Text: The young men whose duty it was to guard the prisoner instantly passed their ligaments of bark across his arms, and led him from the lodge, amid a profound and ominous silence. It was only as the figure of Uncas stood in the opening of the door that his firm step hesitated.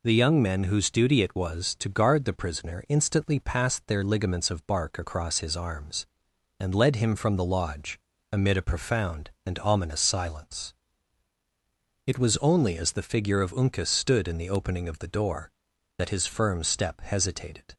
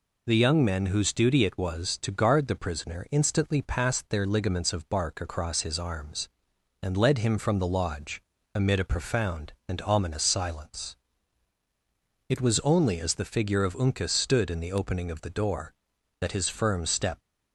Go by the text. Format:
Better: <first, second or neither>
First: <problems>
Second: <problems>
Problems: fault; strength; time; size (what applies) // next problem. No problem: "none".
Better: first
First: none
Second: stops before "hesitated"; at 17.2 s